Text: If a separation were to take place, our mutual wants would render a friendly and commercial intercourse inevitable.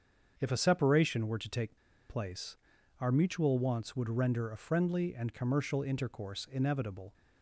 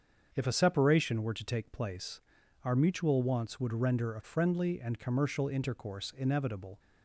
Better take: second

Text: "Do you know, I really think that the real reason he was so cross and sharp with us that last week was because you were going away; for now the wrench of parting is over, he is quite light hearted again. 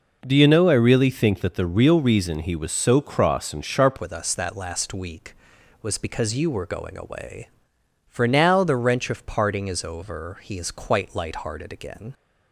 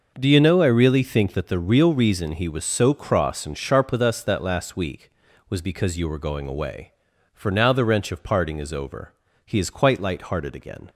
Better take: second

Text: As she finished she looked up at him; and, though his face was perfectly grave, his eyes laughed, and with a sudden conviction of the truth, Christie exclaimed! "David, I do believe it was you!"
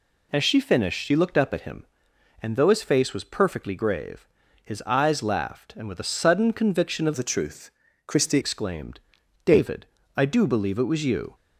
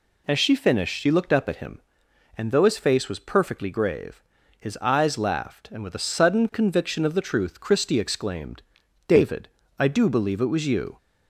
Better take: second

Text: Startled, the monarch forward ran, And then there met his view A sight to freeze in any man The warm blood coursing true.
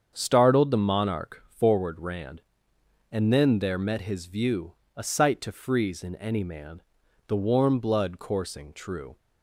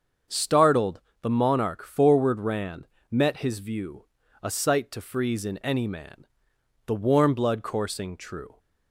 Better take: first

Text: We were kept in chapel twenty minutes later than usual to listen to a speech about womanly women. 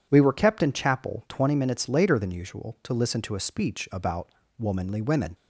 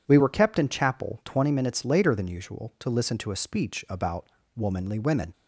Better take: neither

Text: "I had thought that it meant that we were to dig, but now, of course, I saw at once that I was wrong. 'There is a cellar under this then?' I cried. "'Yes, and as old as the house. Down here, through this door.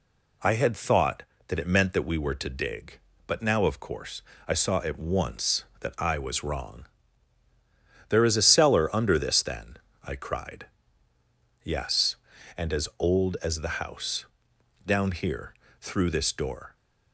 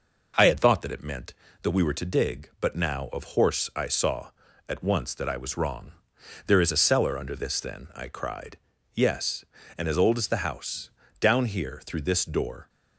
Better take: first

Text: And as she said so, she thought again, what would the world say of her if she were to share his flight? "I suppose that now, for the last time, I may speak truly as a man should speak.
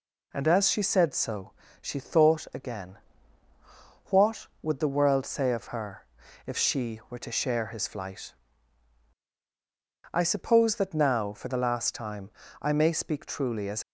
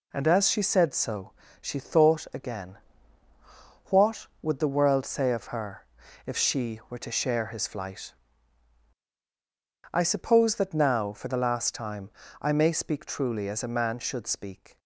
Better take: second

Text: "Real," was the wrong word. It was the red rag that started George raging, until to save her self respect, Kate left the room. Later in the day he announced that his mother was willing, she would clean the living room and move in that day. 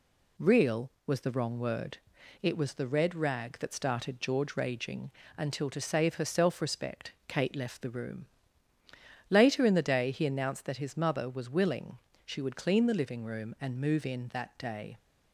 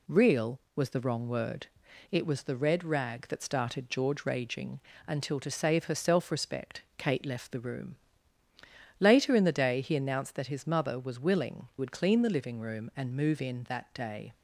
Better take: first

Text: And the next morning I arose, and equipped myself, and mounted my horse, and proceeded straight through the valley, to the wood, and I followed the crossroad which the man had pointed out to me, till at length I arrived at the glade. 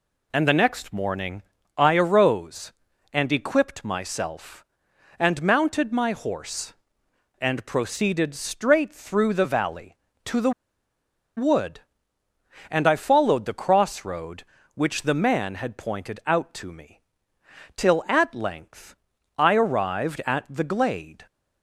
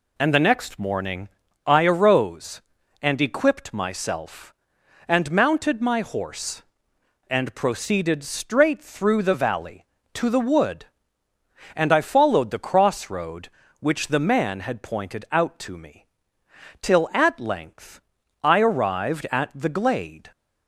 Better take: second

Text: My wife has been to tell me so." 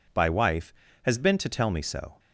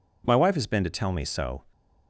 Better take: second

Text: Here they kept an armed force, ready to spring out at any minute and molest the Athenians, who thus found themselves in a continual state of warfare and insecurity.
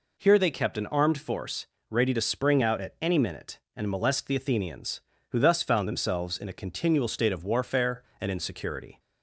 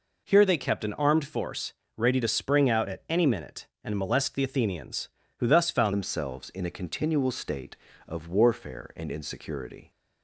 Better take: first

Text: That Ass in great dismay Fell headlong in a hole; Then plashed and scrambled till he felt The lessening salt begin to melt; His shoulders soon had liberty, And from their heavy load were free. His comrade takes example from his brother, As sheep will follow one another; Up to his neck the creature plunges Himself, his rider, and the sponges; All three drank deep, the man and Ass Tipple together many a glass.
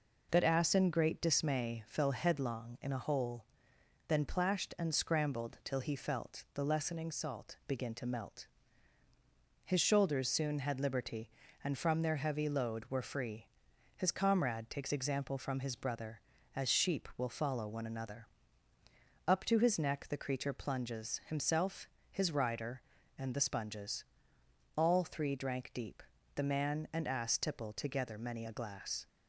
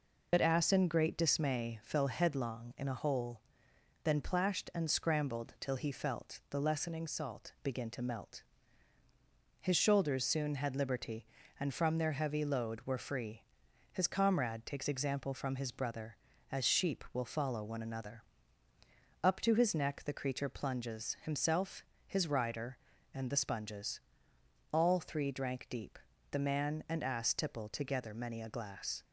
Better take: first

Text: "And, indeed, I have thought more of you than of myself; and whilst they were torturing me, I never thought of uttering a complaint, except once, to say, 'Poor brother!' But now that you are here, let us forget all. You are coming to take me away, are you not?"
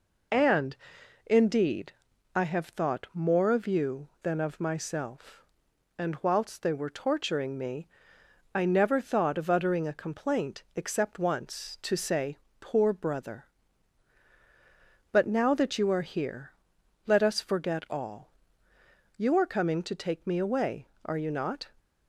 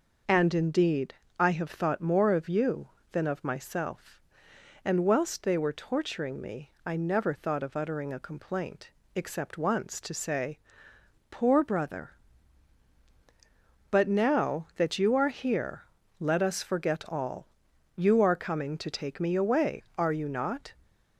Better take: neither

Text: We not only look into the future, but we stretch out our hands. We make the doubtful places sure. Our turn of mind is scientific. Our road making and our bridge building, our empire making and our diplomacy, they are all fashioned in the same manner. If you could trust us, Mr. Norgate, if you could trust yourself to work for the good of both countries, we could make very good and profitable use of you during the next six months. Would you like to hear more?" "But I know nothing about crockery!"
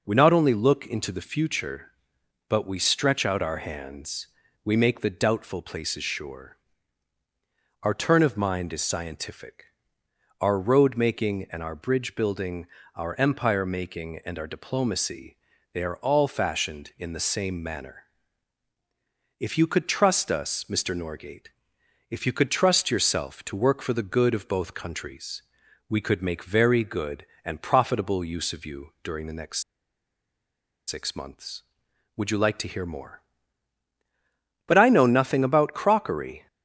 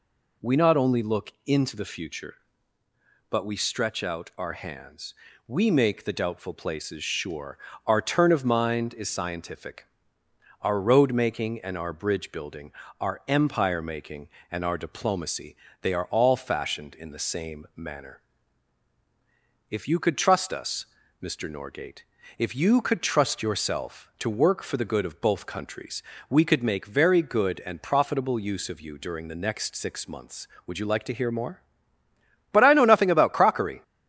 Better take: second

